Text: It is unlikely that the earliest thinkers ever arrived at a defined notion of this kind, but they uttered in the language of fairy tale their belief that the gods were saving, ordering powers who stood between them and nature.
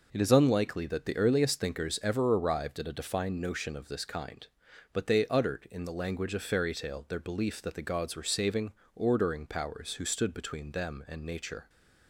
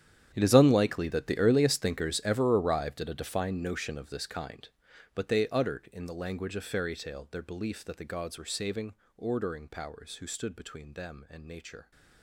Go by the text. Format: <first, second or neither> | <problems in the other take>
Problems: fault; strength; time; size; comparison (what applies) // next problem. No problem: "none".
first | gets quieter; strong; throughout; 17 dB